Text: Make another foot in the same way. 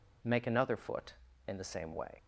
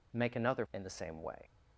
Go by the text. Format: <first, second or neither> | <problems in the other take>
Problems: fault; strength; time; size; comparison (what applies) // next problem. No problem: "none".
first | skips "foot"; at 0.6 s